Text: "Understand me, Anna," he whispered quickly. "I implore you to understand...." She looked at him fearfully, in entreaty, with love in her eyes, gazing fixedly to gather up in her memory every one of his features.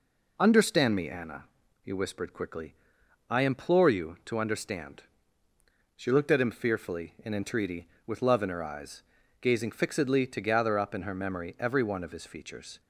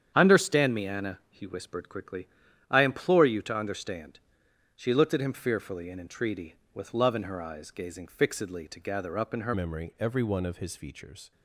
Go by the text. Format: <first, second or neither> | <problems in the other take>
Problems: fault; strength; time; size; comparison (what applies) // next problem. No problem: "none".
first | starts louder than the rest; strong; until 1.1 s; 8.5 dB // changes voice at "memory"; from 9.5 s on; 1.8 s long